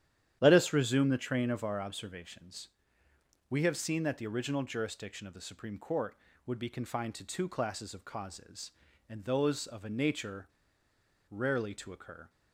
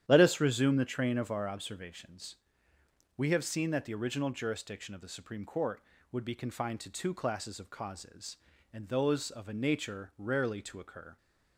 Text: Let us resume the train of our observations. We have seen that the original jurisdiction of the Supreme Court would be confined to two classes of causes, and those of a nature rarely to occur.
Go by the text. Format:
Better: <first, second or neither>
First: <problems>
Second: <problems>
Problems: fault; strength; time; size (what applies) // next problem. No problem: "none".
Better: second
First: starts louder than the rest; strong; until 1.4 s; 10.5 dB // pauses between "nature" and "rarely"; noticeable; at 10.4 s; 0.82 s long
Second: starts louder than the rest; strong; until 1.0 s; 10.5 dB